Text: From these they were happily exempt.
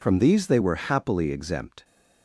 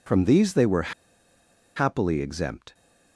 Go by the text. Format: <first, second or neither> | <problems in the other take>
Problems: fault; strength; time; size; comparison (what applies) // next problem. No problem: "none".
first | pauses between "were" and "happily"; noticeable; at 0.9 s; 0.84 s long